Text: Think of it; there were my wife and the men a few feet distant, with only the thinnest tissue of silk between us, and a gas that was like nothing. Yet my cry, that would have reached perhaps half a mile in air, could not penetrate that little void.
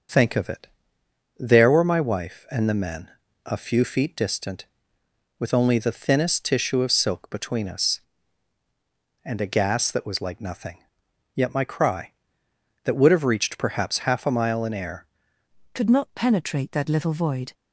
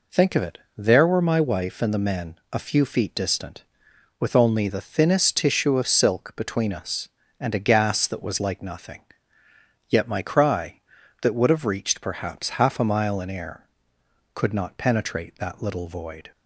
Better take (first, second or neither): second